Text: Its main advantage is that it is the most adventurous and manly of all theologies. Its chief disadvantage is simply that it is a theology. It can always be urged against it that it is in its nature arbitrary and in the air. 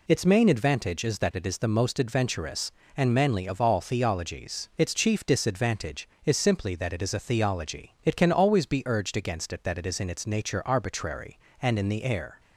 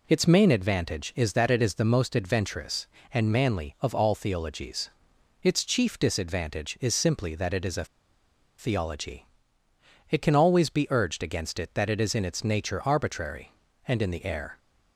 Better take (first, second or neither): first